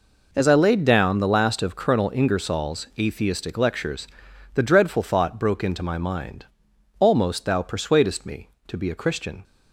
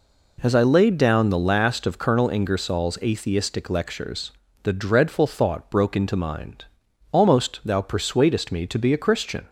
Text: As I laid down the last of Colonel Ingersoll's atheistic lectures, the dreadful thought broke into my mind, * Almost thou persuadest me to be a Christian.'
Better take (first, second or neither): first